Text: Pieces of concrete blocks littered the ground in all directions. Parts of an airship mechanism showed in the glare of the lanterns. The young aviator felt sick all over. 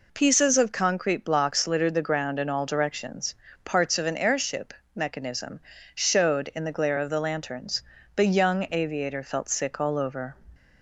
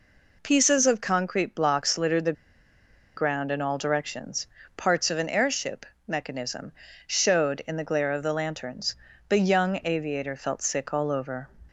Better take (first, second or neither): first